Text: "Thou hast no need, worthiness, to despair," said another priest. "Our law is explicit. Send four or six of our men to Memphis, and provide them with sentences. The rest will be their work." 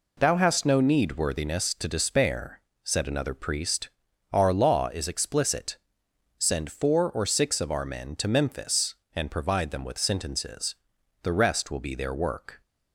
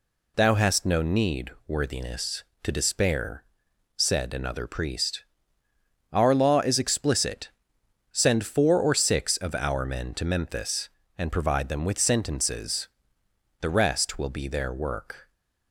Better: neither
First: none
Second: none

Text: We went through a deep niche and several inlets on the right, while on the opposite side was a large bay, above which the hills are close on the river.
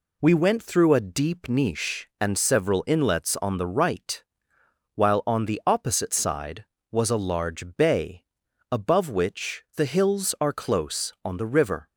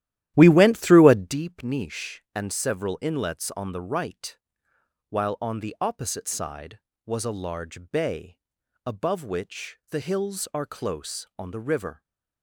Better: first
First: none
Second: starts louder than the rest; strong; until 1.4 s; 13 dB

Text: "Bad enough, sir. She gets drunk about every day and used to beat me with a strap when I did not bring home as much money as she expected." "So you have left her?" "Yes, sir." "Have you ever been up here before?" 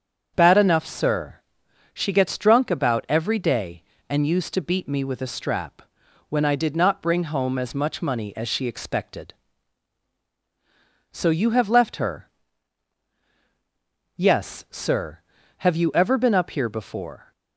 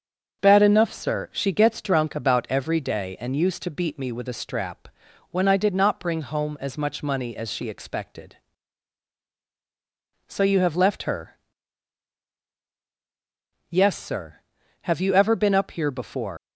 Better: first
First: starts louder than the rest; strong; until 1.3 s; 7 dB // pauses between "strap" and "when"; noticeable; at 5.8 s; 0.46 s long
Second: starts louder than the rest; until 1.4 s; 6.5 dB // pauses between "strap" and "when"; at 4.8 s; 0.44 s long // leaves "before" unfinished; at 16.3 s; 140 ms

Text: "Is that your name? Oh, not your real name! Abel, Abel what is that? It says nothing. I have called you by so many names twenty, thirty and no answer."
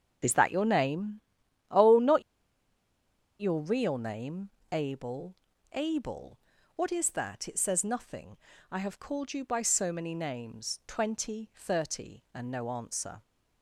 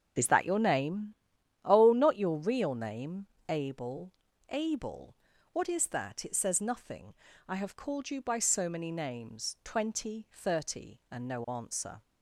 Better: second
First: starts louder than the rest; until 1.7 s; 6.5 dB // pauses between "not" and "your"; at 2.2 s; 1.1 s long // pauses between "Abel" and "what"; at 6.3 s; 0.40 s long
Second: starts louder than the rest; until 1.6 s; 6.5 dB // pauses between "Abel" and "what"; at 5.1 s; 0.40 s long

